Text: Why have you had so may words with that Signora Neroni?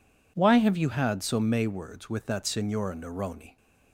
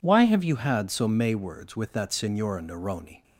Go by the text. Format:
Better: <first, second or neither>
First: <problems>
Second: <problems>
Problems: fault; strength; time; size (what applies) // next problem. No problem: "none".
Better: neither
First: none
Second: none